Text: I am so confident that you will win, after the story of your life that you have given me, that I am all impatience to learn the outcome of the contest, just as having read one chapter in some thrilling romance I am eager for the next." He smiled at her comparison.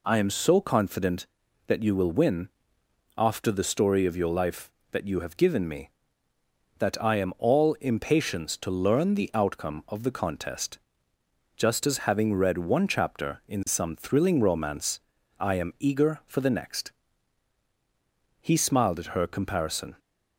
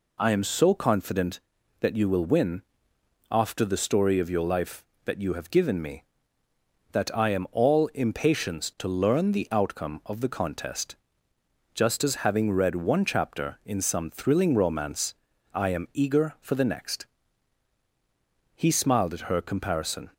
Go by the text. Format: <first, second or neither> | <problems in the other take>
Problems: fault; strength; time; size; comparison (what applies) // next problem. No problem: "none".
neither | pauses between "romance" and "I"; the same in both